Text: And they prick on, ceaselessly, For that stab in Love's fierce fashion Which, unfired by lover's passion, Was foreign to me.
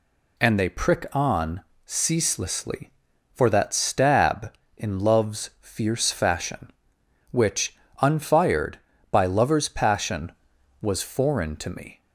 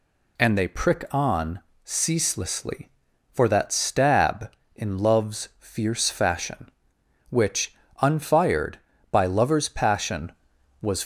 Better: first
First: none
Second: stops before "foreign to me"; at 11.0 s

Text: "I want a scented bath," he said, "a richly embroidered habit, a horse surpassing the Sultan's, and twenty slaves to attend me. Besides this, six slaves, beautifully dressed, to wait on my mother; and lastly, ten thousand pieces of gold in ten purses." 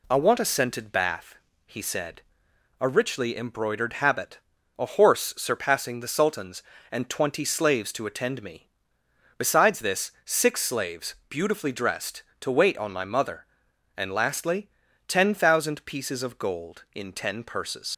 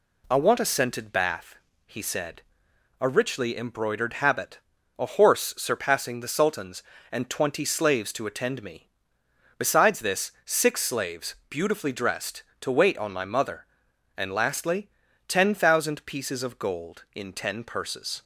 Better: second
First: leaves "purses" unfinished; at 17.9 s; 80 ms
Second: none

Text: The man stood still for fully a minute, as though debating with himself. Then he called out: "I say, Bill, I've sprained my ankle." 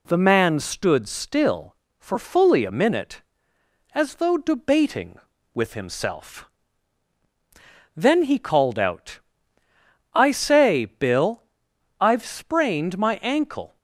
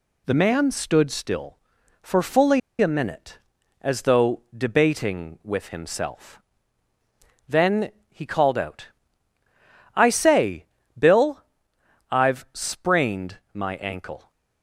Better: first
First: none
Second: pauses between "fully" and "a"; slight; at 2.5 s; 0.21 s long // pauses between "Then" and "he"; slight; at 7.8 s; 0.20 s long // pauses between "sprained" and "my"; slight; at 13.3 s; 0.16 s long

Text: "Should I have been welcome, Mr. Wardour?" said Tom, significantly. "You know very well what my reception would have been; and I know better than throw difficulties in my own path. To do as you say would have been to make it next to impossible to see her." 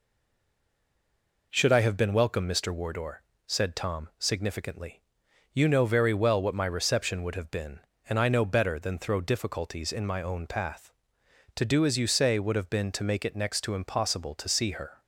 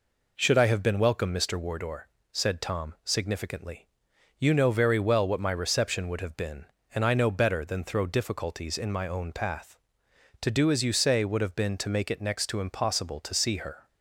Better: second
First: stays silent before the first word; noticeable; until 1.5 s; 1.5 s long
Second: none

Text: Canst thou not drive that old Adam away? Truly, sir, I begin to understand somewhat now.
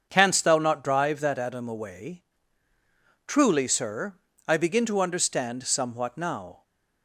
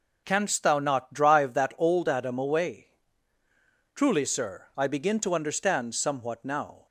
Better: second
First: starts louder than the rest; until 1.1 s; 7 dB // skips "old"; at 1.3 s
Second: none

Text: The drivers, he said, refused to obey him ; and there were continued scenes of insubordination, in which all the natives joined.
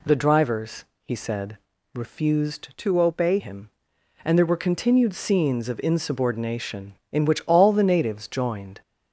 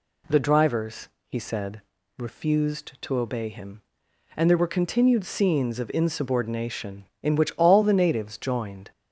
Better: second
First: changes voice from "to" to "obey"; from 2.7 to 3.3 s; 0.6 s long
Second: none

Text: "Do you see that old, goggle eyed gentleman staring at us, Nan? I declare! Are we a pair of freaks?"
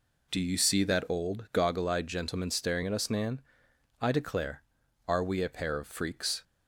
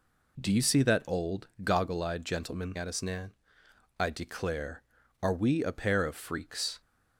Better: first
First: none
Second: skips "staring"; at 2.7 s

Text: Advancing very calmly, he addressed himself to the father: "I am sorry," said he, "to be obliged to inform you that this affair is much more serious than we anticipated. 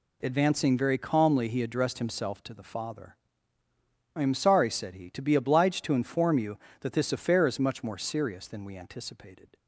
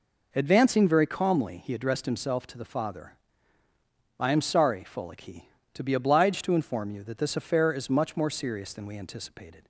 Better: first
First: none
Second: says "folic" for "said"; at 4.8 s

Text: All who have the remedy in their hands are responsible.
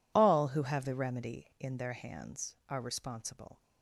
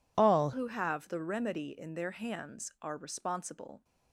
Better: first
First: none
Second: changes voice at "who"; from 0.5 s on; 3.3 s long

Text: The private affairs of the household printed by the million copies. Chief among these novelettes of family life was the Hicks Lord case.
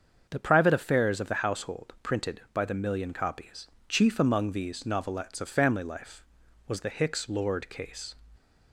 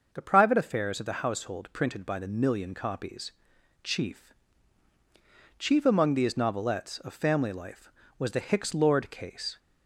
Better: first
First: starts louder than the rest; until 1.3 s; 7 dB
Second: starts louder than the rest; until 1.1 s; 6 dB // says "Chief" twice; at 5.5 s

